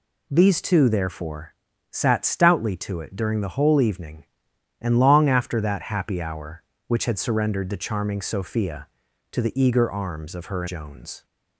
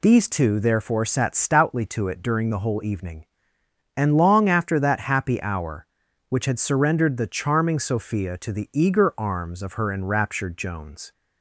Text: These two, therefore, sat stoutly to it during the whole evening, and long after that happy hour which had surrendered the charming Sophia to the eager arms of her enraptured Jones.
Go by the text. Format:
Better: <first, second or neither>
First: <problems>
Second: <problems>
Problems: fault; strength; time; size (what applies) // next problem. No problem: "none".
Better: second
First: skips "enraptured"; at 10.6 s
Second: none